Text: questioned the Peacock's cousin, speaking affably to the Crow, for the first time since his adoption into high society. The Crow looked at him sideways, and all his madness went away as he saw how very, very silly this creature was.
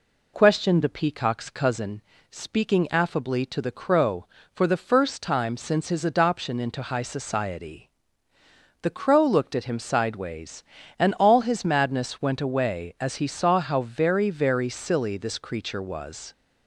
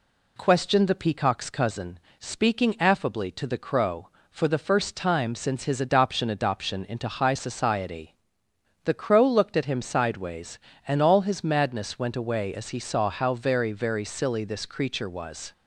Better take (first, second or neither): first